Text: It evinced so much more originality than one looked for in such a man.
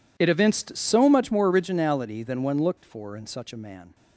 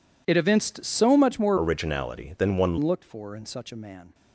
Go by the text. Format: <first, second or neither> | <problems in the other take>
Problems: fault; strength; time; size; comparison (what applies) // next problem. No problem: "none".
first | changes voice from "originality" to "one"; from 1.5 to 2.7 s; 1.2 s long